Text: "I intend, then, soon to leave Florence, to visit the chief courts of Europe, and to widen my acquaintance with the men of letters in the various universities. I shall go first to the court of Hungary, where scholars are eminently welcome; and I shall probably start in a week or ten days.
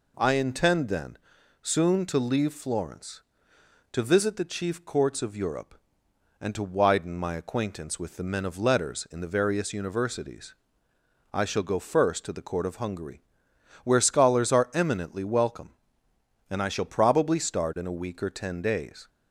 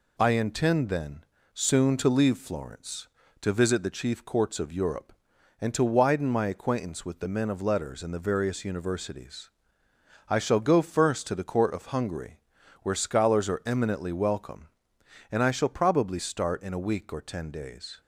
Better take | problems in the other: neither | none

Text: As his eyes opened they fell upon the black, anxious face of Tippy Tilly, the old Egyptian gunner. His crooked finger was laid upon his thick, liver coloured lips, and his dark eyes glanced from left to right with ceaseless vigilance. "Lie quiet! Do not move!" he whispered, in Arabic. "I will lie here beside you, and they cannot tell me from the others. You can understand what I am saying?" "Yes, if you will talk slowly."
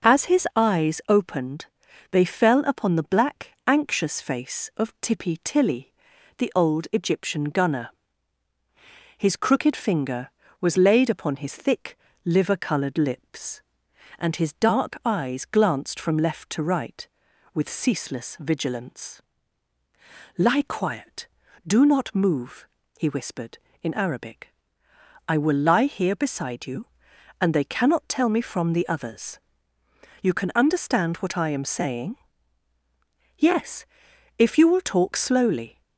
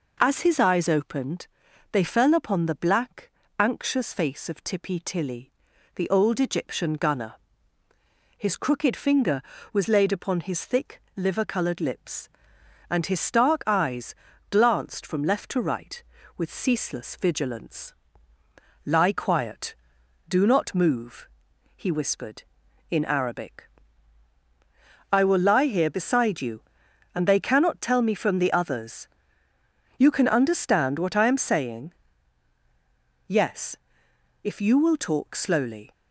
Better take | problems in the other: first | pauses between "opened" and "they"; at 1.4 s; 0.44 s long; also in the first // says "stark" for "dark"; at 13.2 s // pauses between "eyes" and "glanced"; slight; at 14.1 s; 0.36 s long

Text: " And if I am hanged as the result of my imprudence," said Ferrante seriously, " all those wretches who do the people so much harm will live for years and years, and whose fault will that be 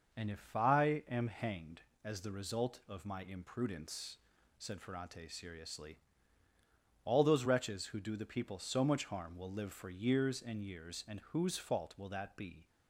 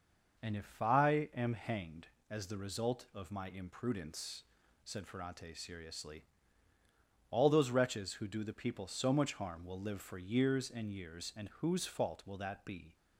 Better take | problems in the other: neither | none

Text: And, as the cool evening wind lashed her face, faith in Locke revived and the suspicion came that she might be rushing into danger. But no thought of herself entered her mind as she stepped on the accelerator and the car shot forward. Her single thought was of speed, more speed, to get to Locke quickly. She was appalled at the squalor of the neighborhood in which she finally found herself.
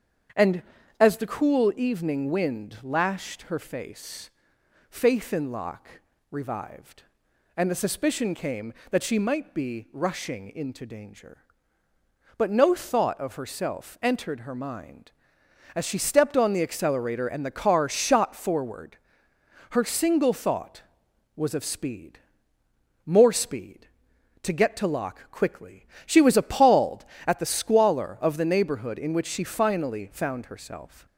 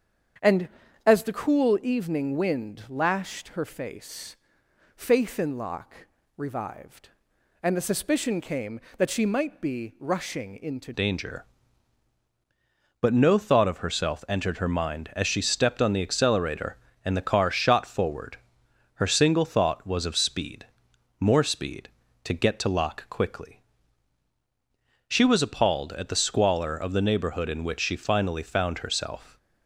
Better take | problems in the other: first | starts louder than the rest; strong; until 1.7 s; 8 dB; strong in the first // pauses between "Locke" and "revived"; slight; at 6.0 s; 0.30 s long; slight in the first // changes voice at "danger"; from 10.9 s on; 18.4 s long

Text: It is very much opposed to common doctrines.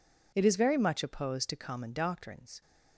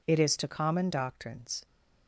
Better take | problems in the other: first | skips "very much opposed"; at 0.3 s

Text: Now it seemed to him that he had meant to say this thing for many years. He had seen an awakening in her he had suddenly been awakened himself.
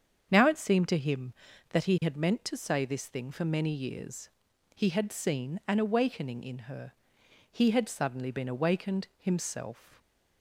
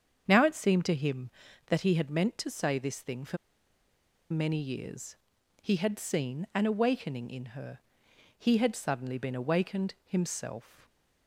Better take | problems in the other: first | starts louder than the rest; strong; until 1.2 s; 7.5 dB; strong in the first // pauses between "for" and "many"; noticeable; at 3.3 s; 0.93 s long // pauses between "her" and "he"; noticeable; at 7.7 s; 0.60 s long; noticeable in the first

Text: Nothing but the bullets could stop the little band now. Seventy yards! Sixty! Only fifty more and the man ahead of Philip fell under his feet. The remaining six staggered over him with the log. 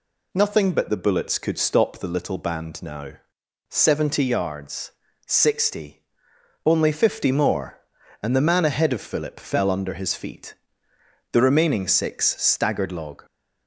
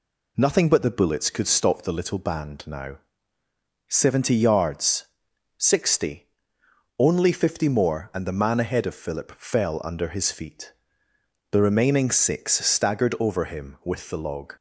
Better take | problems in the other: second | skips "over him with the"; at 12.8 s

